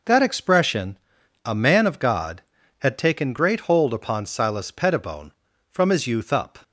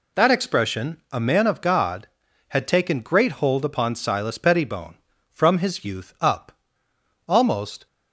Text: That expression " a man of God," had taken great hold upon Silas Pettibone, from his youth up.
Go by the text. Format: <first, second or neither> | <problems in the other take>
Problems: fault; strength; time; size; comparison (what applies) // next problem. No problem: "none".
first | goes on to say "Almost"; from 7.2 s on; 0.60 s long